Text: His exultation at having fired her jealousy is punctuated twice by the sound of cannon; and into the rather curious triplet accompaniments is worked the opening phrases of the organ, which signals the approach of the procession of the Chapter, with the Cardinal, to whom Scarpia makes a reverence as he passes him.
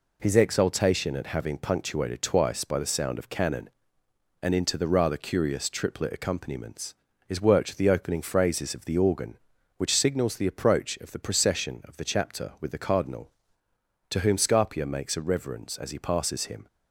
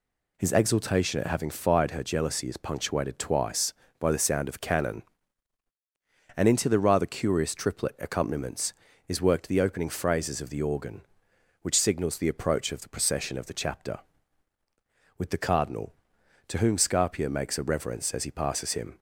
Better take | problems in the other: second | skips "fired her jealousy is"; at 1.5 s

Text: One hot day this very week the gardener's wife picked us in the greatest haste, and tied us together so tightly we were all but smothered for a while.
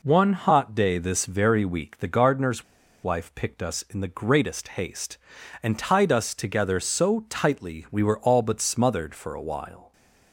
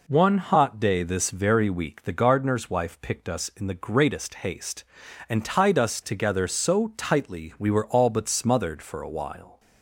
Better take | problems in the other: second | pauses between "gardener's" and "wife"; at 2.6 s; 0.39 s long

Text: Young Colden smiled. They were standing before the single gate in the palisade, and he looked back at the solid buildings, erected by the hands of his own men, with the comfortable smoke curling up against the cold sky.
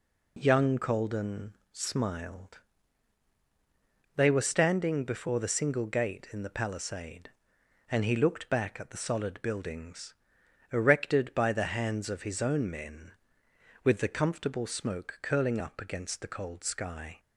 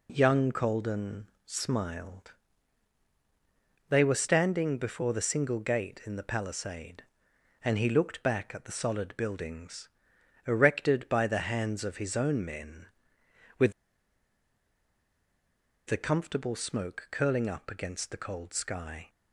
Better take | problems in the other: first | pauses between "Colden" and "smiled"; slight; at 1.2 s; 0.16 s long; slight in the first // pauses between "with" and "the"; strong; at 13.7 s; 2.1 s long

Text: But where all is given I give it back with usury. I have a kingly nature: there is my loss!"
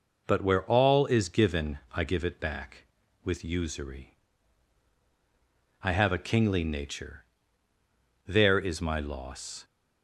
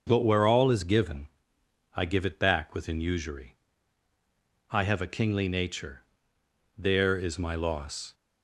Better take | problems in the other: first | starts louder than the rest; until 1.0 s; 6 dB // pauses between "given" and "I"; noticeable; at 1.2 s; 0.66 s long // says "within" for "with"; at 2.7 s

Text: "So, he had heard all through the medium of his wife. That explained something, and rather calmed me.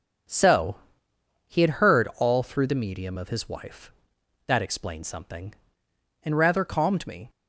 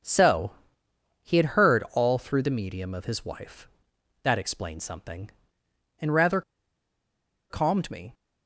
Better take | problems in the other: first | pauses between "rather" and "calmed"; at 6.4 s; 1.0 s long

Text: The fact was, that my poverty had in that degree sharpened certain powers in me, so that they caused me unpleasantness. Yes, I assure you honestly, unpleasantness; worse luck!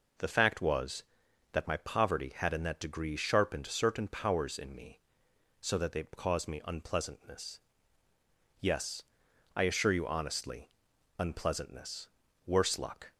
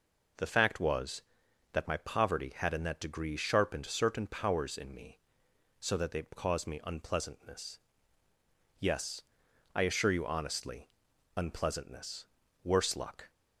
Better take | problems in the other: neither | none

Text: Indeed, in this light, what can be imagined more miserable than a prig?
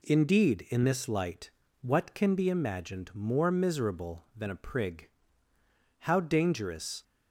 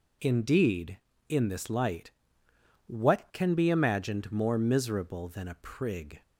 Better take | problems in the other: second | goes on to say "How dangerous"; noticeable; from 5.9 s on; 1.0 s long

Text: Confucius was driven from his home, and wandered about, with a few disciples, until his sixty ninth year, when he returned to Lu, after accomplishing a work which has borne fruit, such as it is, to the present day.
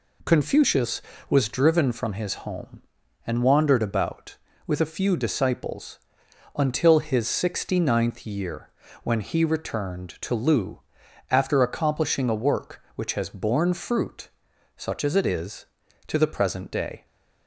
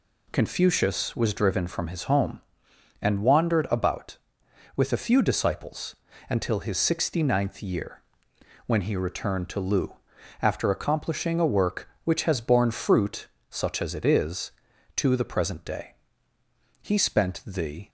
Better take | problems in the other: first | goes on to say "He spent the"; noticeable; from 16.8 s on; 1.0 s long

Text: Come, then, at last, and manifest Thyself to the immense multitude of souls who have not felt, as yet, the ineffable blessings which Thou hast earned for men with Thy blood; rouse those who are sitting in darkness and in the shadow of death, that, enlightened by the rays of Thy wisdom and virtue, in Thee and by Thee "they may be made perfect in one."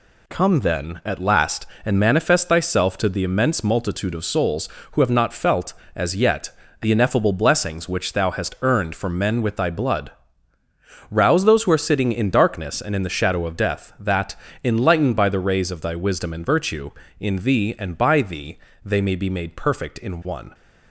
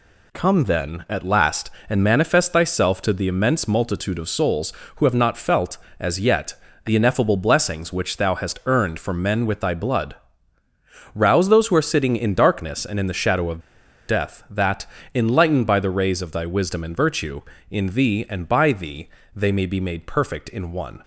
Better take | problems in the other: first | pauses between "of" and "death"; noticeable; at 13.5 s; 0.48 s long // pauses between "Thee" and "they"; slight; at 19.0 s; 0.26 s long; slight in the first

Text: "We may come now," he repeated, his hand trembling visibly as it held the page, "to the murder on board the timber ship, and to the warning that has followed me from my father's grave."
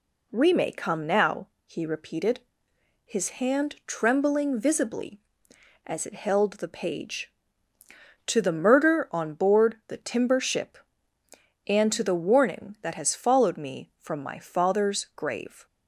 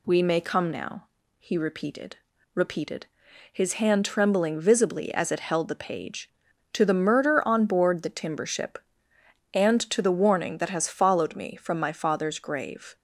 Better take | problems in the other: first | says "repeated" twice; at 2.5 s

